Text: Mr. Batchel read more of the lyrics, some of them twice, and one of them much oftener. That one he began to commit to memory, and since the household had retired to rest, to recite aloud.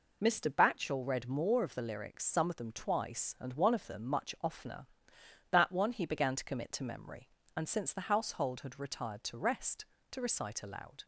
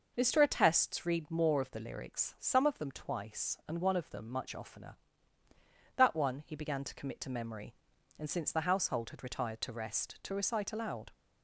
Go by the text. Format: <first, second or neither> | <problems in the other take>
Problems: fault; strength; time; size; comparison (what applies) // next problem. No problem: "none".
first | says "Attests" for "Batchel"; at 0.4 s